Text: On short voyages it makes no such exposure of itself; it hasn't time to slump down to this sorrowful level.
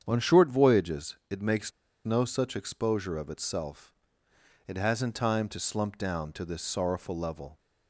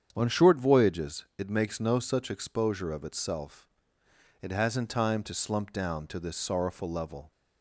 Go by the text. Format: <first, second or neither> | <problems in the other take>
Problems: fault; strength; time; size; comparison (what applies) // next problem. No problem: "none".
second | starts louder than the rest; strong; until 1.0 s; 8 dB; strong in the second // pauses between "voyages" and "it"; slight; at 1.1 s; 0.16 s long; slight in the second // pauses between "makes" and "no"; slight; at 1.7 s; 0.34 s long